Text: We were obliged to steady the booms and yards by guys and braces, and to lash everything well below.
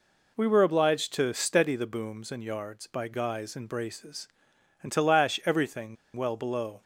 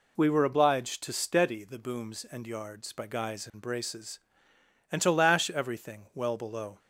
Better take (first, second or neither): second